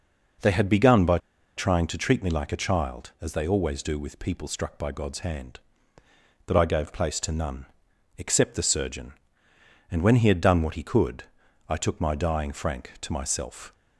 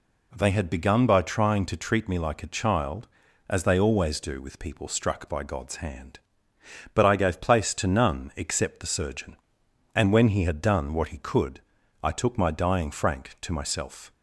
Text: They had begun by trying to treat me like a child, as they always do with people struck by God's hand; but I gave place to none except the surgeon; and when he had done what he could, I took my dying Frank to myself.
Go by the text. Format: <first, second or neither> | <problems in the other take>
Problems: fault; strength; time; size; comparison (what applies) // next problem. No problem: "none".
second | pauses between "by" and "trying"; at 1.1 s; 0.38 s long // pauses between "none" and "except"; noticeable; at 7.6 s; 0.50 s long